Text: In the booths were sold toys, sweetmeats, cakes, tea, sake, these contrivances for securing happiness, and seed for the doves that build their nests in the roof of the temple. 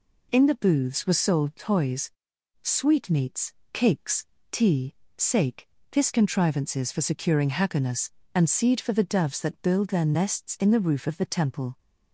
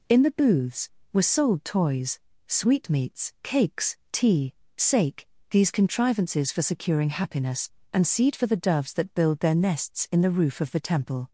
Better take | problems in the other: second | says "this" for "these"; at 5.8 s

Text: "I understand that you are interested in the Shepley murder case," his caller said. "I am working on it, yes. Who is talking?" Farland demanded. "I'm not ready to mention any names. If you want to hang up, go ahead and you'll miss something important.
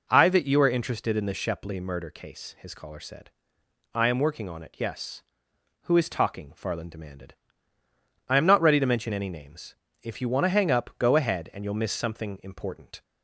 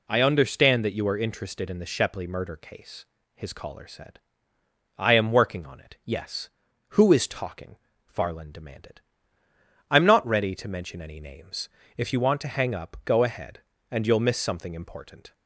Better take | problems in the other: second | skips "understand"; at 0.2 s

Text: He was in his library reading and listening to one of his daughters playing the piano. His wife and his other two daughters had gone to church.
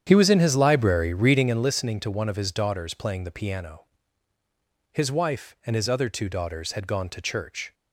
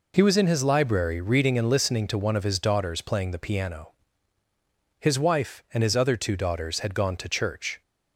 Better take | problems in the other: second | starts louder than the rest; strong; until 1.7 s; 9 dB

